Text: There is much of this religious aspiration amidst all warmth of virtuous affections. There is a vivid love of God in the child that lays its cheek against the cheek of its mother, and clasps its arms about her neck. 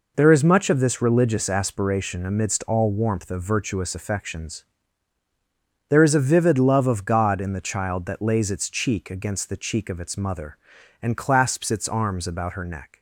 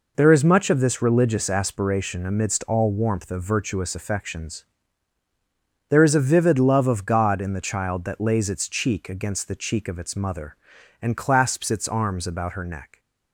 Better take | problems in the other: neither | none

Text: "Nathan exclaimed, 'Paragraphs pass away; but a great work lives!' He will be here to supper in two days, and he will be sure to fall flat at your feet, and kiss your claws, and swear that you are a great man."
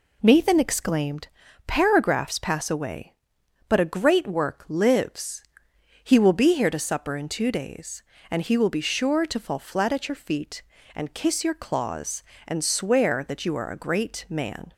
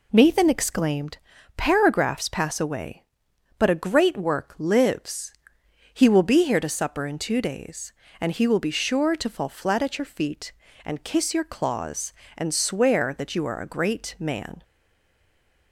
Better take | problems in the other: first | stays silent after the last word; from 14.6 s on; 1.1 s long

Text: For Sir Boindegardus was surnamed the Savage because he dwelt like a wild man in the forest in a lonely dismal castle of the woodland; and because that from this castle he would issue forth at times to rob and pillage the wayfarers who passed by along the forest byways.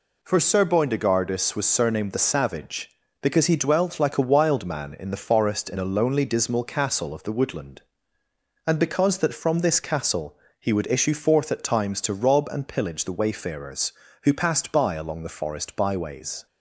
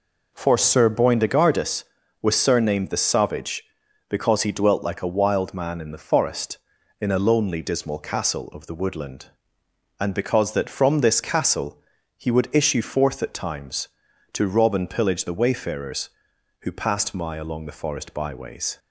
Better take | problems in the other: first | pauses between "castle" and "he"; slight; at 11.8 s; 0.34 s long; slight in the first // says "my" for "by"; at 17.1 s

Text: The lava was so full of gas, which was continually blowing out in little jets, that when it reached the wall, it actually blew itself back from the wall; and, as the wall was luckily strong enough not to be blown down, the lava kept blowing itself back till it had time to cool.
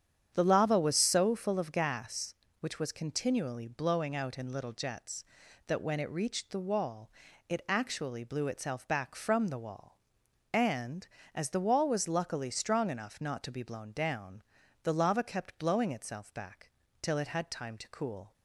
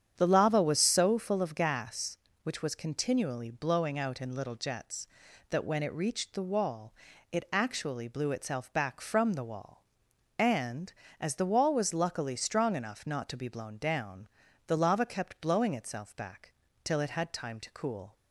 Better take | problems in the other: neither | starts louder than the rest; strong; the same in both // pauses between "back" and "till"; slight; the same in both

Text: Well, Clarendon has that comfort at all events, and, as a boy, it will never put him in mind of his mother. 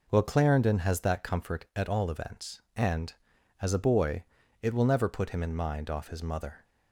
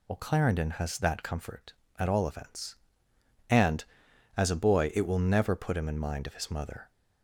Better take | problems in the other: second | says "off" for "of"; at 5.8 s

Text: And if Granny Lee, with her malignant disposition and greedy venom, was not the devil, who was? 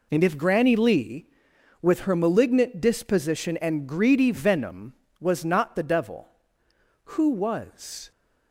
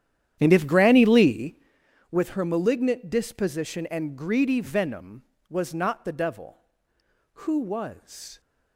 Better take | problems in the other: first | starts louder than the rest; strong; until 1.8 s; 10.5 dB

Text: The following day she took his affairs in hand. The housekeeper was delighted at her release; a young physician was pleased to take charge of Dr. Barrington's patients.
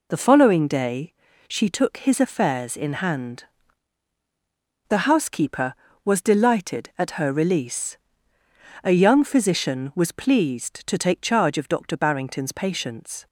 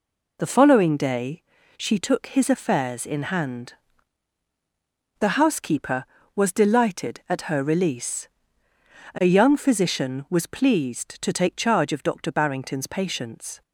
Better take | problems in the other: neither | pauses between "day" and "she"; slight; the same in both

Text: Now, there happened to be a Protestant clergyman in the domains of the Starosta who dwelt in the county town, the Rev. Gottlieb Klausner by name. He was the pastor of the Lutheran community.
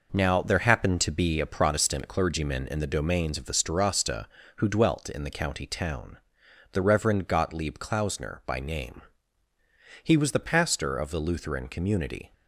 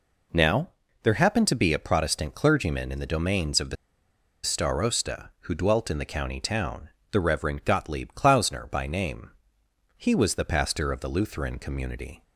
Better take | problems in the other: first | pauses between "the" and "Starosta"; noticeable; at 3.7 s; 0.69 s long

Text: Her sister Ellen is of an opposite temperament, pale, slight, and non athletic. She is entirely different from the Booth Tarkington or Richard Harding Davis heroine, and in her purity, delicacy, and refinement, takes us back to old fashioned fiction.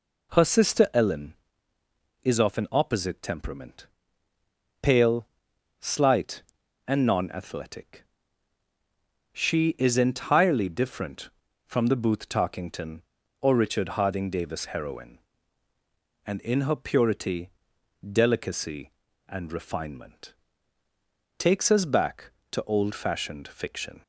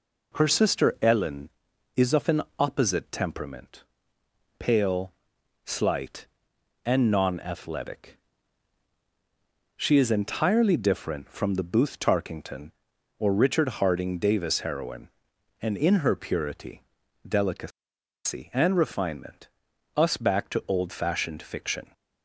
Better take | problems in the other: first | pauses between "an" and "opposite"; slight; at 2.4 s; 0.18 s long // skips "takes"; at 19.7 s

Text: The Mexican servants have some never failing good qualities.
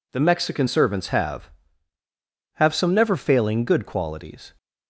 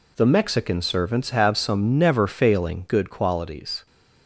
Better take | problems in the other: second | says "have" twice; at 2.5 s

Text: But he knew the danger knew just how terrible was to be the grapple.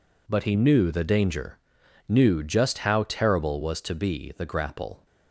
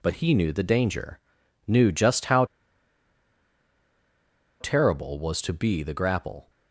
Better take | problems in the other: first | pauses between "danger" and "knew"; noticeable; at 1.1 s; 0.48 s long; noticeable in the first // pauses between "how" and "terrible"; strong; at 2.4 s; 2.1 s long

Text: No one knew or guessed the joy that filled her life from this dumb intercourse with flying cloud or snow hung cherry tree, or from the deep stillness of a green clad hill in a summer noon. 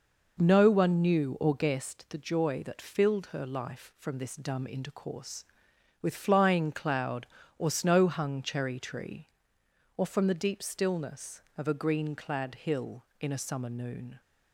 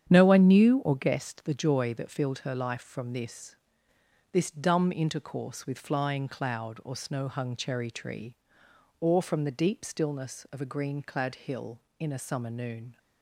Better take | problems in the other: first | starts louder than the rest; strong; until 1.1 s; 9 dB // says "this" twice; at 4.3 s

